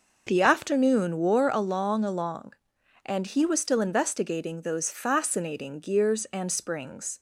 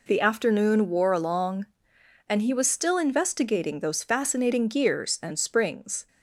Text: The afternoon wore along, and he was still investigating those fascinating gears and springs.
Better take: second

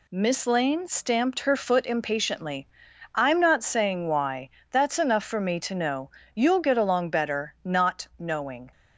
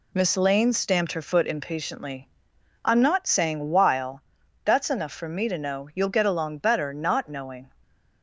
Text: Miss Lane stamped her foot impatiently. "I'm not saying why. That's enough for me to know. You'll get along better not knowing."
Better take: first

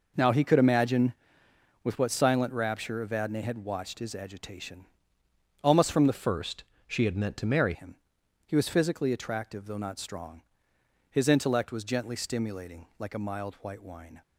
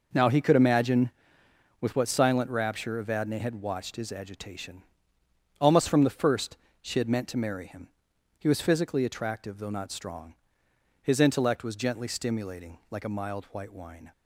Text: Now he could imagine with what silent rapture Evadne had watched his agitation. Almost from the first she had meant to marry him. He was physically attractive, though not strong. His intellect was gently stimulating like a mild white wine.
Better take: second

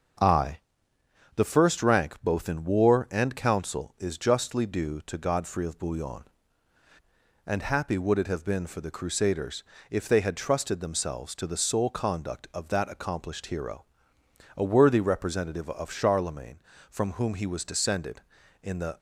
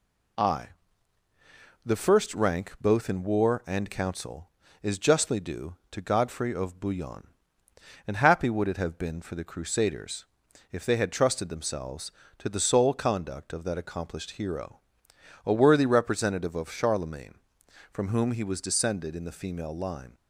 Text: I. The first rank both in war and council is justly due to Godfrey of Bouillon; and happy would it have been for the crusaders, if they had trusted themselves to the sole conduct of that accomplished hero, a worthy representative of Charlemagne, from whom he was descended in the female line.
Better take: second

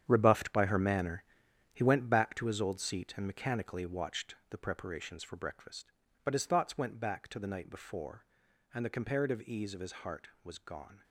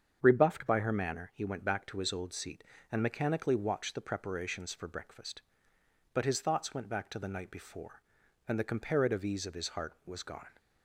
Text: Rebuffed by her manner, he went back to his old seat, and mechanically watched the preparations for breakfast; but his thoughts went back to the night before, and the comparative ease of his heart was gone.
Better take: second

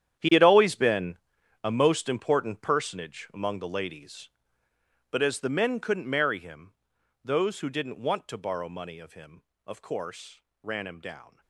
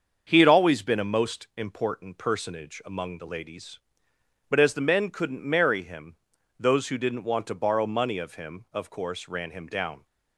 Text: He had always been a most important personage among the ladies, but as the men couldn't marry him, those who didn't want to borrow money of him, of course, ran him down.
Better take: second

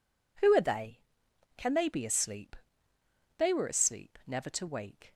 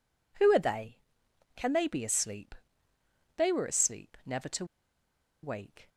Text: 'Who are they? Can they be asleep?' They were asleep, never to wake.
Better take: first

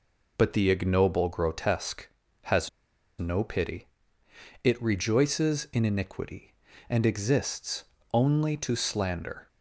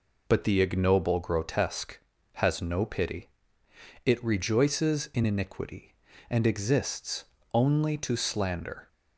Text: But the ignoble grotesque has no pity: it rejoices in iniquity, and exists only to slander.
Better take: second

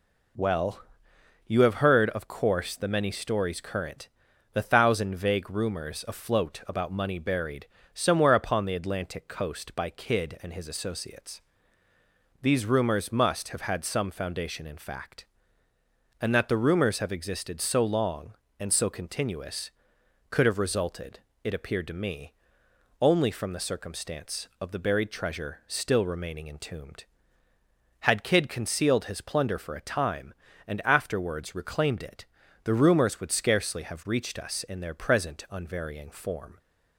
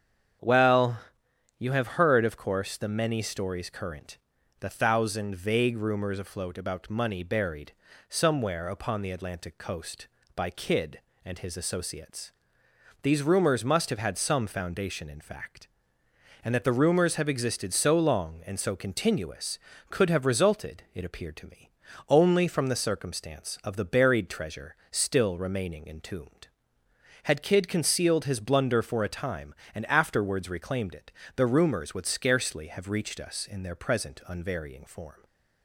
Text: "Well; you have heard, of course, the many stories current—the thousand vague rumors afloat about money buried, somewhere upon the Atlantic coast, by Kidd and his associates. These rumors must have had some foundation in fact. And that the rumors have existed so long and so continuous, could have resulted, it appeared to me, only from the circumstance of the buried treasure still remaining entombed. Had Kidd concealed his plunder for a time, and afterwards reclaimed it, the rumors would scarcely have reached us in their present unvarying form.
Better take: first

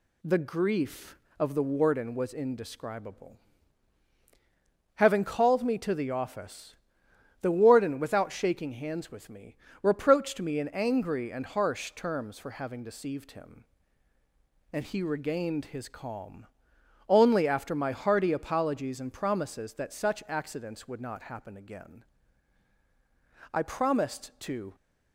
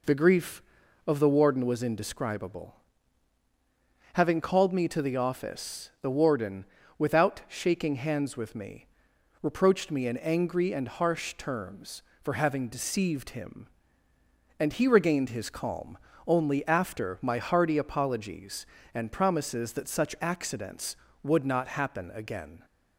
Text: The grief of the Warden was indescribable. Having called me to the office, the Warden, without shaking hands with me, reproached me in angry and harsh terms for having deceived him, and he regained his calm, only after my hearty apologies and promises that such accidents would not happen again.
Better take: second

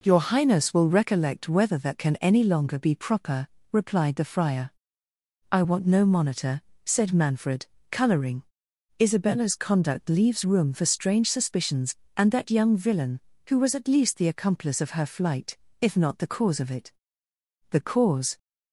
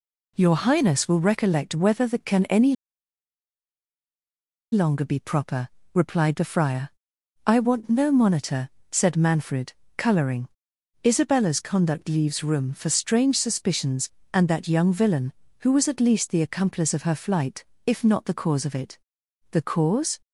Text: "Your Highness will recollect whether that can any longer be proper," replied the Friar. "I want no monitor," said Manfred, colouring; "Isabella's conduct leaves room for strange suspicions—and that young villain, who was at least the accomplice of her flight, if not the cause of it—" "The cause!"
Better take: first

